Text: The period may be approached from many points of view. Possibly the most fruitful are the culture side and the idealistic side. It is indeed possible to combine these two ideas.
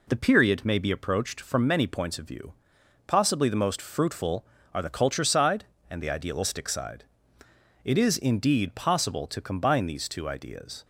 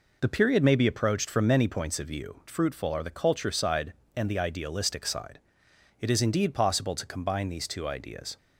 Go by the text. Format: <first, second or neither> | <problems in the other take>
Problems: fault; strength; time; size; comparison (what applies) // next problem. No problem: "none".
first | skips "Possibly the most"; at 2.4 s